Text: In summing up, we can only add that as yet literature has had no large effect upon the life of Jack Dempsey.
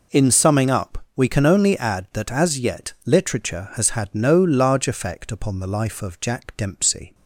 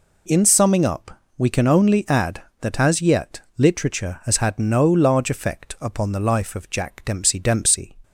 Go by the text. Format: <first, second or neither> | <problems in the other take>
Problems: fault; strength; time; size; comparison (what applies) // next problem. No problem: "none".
first | pauses between "yet" and "literature"; slight; at 3.4 s; 0.16 s long // says "Dempsey" twice; at 7.3 s